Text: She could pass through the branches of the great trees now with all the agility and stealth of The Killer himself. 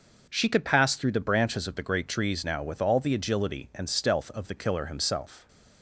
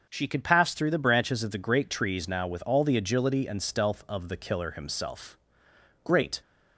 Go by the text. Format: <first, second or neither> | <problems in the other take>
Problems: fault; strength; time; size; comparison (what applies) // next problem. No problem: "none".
first | starts louder than the rest; until 1.0 s; 6 dB // goes on to say "Great"; slight; from 6.0 s on; 0.38 s long